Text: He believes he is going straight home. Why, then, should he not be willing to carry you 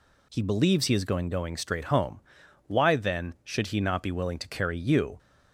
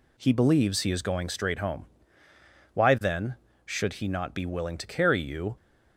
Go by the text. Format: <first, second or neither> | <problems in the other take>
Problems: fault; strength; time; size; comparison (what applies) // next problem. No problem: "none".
second | says "going" twice; at 1.3 s